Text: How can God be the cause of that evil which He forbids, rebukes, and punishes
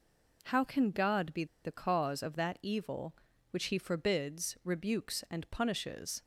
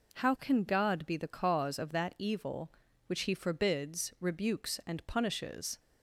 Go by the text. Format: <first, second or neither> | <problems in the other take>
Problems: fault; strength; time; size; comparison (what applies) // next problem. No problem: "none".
second | pauses between "be" and "the"; slight; at 1.4 s; 0.19 s long